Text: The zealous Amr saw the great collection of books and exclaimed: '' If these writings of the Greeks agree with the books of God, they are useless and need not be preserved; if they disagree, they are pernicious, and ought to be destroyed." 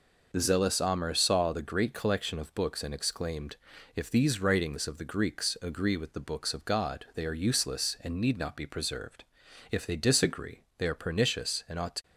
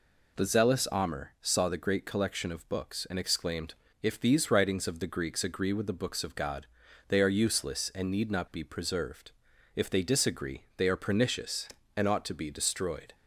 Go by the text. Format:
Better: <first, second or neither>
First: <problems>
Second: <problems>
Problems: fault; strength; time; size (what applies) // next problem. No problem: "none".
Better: second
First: stops before "be destroyed"; at 12.0 s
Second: none